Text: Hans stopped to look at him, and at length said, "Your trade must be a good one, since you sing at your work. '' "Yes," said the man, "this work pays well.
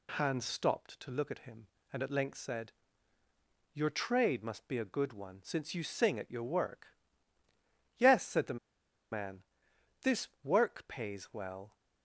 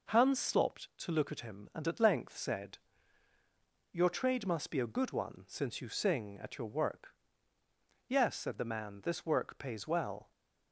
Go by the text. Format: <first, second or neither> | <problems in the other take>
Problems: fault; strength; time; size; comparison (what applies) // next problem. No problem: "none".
second | pauses between "the" and "man"; noticeable; at 8.5 s; 0.54 s long